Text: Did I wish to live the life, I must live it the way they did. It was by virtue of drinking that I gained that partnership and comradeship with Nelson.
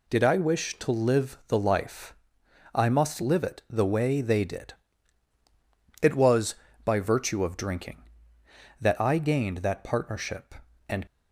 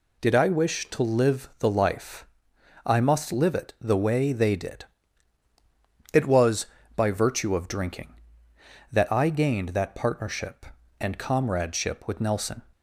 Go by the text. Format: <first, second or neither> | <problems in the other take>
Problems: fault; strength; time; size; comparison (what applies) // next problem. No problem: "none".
second | stops before "comradeship with Nelson"; at 11.0 s